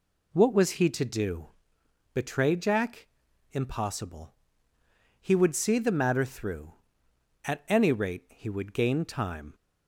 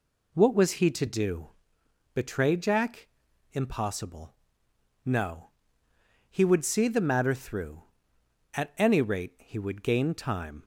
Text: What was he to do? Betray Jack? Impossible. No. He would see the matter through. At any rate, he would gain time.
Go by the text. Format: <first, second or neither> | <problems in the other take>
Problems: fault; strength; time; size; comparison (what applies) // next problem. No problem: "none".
second | skips "No"; at 4.7 s